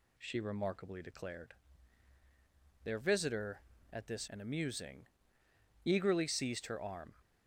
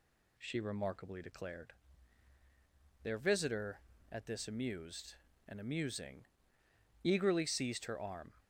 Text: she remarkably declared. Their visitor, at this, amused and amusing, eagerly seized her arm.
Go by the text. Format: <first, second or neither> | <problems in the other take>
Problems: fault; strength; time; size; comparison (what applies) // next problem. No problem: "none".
second | skips "amused"; at 4.2 s